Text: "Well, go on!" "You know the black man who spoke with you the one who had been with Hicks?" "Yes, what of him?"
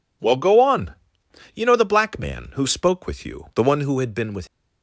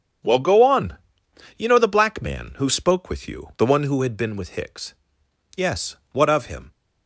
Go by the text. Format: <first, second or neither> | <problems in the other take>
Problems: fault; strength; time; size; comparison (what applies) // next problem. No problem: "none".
second | stops before "Hicks Yes what of him"; at 4.4 s